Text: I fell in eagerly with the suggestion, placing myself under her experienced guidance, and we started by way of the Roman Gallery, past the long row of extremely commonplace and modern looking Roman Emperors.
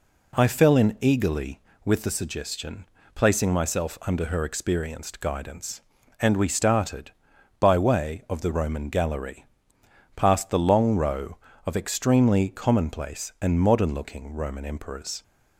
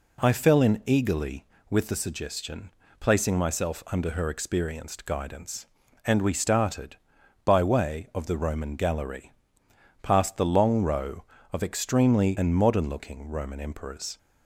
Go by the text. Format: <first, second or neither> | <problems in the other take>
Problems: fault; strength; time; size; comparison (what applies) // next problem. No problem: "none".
first | skips "commonplace"; at 12.3 s